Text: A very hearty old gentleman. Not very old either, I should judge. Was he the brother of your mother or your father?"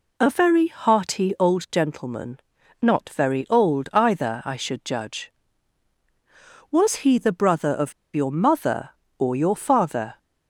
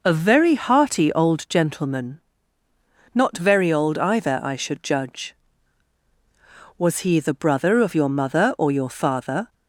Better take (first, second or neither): second